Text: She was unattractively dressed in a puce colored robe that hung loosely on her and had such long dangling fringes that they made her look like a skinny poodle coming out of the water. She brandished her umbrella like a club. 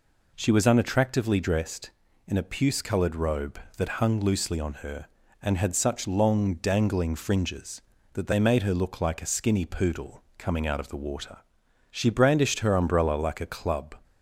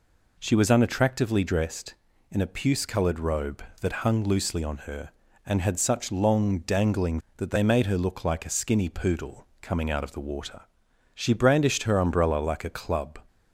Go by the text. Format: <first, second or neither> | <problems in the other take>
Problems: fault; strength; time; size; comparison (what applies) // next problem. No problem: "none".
first | skips "fringes"; at 7.2 s